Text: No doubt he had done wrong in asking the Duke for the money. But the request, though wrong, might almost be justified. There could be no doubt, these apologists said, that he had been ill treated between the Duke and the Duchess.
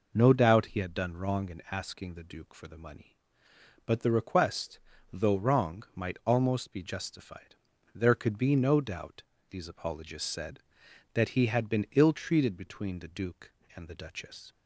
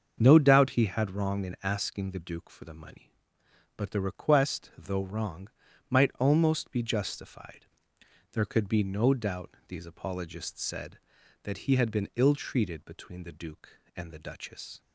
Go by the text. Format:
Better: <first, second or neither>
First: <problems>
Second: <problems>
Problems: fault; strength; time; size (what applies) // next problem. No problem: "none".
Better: first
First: none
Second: starts louder than the rest; until 1.2 s; 7 dB // skips "done"; at 1.1 s